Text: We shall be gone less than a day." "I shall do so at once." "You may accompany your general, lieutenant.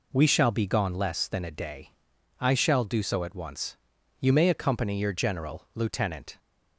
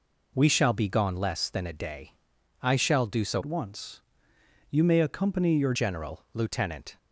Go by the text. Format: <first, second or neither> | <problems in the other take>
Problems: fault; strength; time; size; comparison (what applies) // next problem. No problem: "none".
first | changes voice from "at" to "your"; from 3.3 to 5.7 s; 2.4 s long